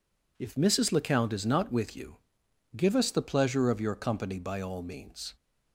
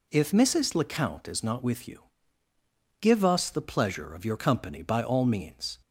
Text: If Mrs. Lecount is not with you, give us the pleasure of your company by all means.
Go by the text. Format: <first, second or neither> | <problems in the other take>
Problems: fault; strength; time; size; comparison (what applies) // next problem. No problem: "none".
neither | none